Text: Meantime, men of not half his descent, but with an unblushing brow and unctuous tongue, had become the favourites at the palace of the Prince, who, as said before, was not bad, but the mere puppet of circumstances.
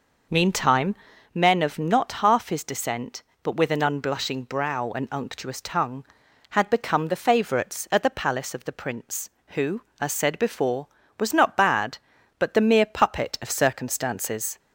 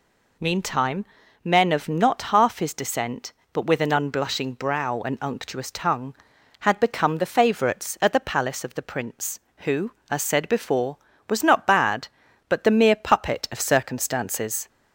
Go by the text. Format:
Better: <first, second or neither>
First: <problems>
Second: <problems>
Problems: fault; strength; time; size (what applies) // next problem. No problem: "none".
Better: second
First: starts louder than the rest; noticeable; until 1.6 s; 5.5 dB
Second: none